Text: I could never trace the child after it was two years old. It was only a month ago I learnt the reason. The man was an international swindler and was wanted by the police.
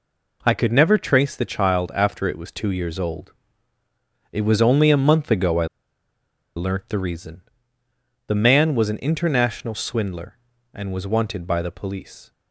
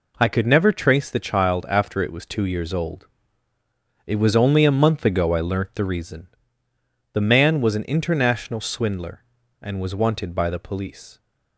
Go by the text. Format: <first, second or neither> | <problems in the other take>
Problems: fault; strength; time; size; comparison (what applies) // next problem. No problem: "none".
second | pauses between "I" and "learnt"; noticeable; at 5.6 s; 0.89 s long